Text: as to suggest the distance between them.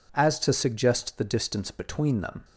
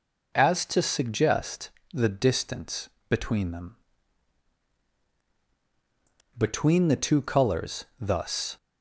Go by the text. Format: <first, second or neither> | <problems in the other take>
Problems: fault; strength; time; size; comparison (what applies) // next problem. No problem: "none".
first | pauses between "suggest" and "the"; slight; at 1.6 s; 0.24 s long // pauses between "distance" and "between"; slight; at 2.8 s; 0.20 s long // goes on to say "Between the two colours thus"; strong; from 6.3 s on; 2.2 s long